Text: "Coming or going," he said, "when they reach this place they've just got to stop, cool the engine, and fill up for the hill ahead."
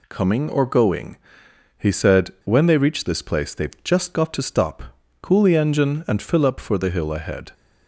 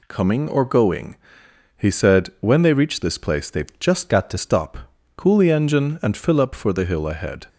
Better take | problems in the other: first | changes voice from "got" to "to"; from 4.0 to 4.3 s; 0.3 s long

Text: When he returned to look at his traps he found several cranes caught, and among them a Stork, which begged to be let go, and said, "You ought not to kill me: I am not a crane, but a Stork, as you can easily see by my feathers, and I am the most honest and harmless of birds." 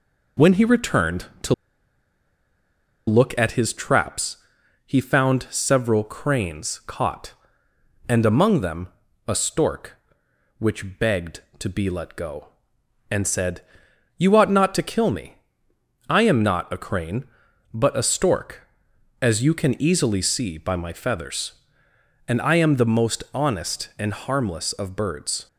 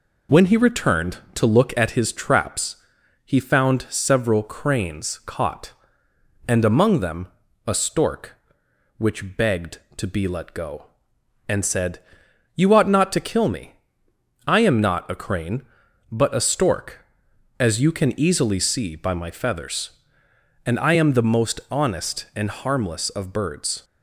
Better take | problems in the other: second | pauses between "to" and "look"; strong; at 1.5 s; 1.5 s long // pauses between "traps" and "he"; noticeable; at 4.3 s; 0.50 s long; noticeable in the second // pauses between "them" and "a"; at 8.8 s; 0.40 s long; also in the second

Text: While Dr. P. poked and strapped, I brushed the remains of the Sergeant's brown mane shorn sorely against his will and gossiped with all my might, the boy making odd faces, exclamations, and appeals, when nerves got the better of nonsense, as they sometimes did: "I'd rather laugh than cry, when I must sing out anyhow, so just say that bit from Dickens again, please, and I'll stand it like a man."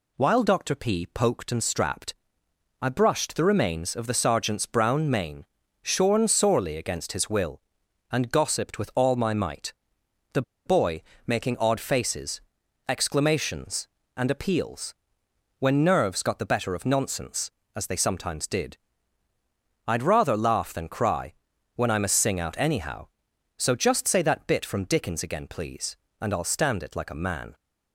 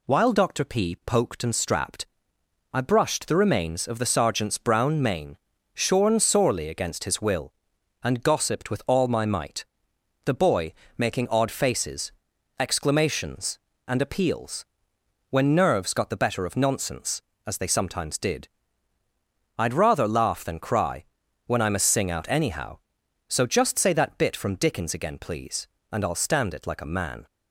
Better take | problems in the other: second | pauses between "mane" and "shorn"; at 5.4 s; 0.38 s long; also in the second // pauses between "the" and "boy"; slight; at 10.4 s; 0.23 s long // pauses between "boy" and "making"; slight; at 11.0 s; 0.22 s long; slight in the second

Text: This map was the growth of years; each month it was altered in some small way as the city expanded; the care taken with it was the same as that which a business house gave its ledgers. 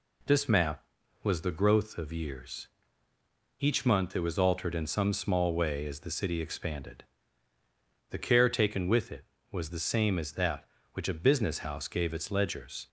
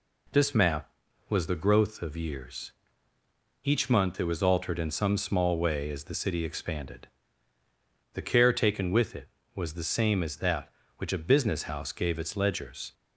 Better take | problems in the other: neither | none

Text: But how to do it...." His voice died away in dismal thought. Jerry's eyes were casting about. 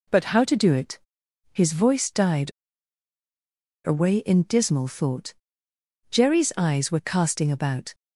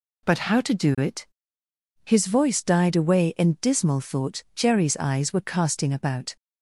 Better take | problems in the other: second | pauses between "died" and "away"; strong; at 2.4 s; 1.3 s long

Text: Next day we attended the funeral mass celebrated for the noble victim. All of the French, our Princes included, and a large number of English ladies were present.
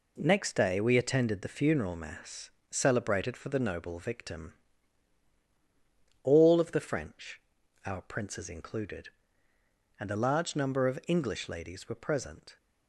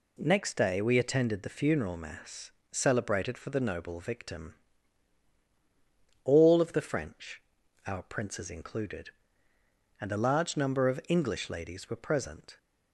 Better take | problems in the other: second | gets quieter; throughout; 6.5 dB // pauses between "mass" and "celebrated"; slight; at 2.4 s; 0.22 s long; slight in the second

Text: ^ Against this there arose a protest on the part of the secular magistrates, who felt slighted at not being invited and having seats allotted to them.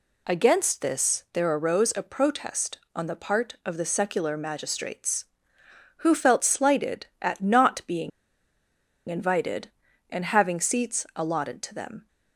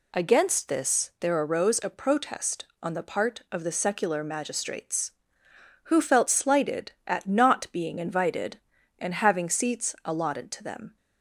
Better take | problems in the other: second | pauses between "being" and "invited"; at 8.1 s; 0.98 s long

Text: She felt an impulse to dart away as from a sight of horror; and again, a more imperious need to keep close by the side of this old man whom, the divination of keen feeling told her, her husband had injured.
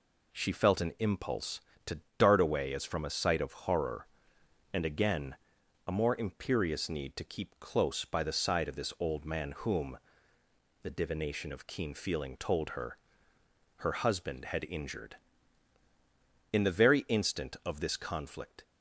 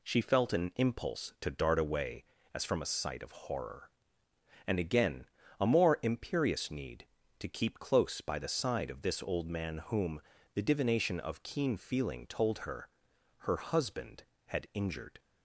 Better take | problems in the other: second | pauses between "to" and "dart"; slight; at 2.0 s; 0.16 s long // goes on to say "In the very instant of this conflict"; strong; from 16.5 s on; 2.1 s long

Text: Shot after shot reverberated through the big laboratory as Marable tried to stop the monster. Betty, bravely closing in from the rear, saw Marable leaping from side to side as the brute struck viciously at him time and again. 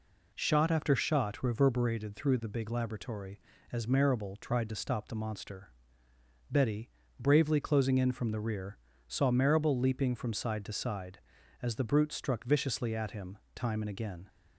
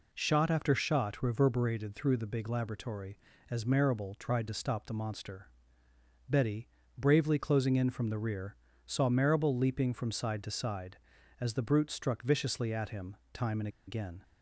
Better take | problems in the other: first | pauses between "him" and "time"; slight; at 13.1 s; 0.16 s long; slight in the first // pauses between "and" and "again"; slight; at 13.6 s; 0.19 s long

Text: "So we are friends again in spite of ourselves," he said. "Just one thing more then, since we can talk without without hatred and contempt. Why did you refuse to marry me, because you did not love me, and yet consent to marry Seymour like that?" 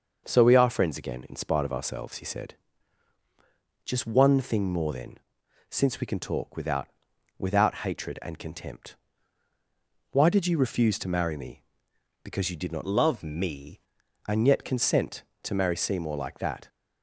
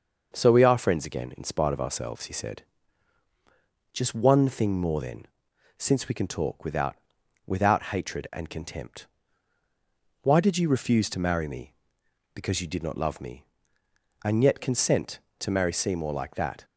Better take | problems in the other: second | starts louder than the rest; until 1.2 s; 6 dB; also in the second // pauses between "without" and "without"; noticeable; at 6.8 s; 0.48 s long; noticeable in the second // changes voice from "love" to "me"; from 12.8 to 13.7 s; 0.9 s long

